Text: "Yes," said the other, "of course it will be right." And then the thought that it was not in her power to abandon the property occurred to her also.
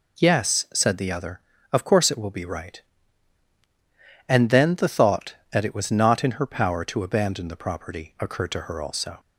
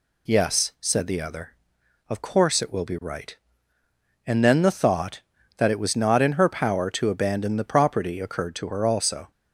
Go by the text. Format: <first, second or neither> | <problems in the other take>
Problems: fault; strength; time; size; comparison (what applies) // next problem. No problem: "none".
neither | none